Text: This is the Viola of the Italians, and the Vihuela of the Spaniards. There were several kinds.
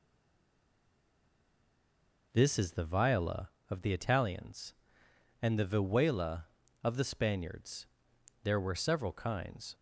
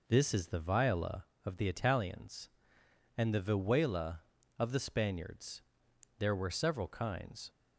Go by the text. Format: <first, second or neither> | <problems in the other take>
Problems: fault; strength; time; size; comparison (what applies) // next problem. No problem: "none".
second | stays silent before the first word; until 2.3 s; 2.3 s long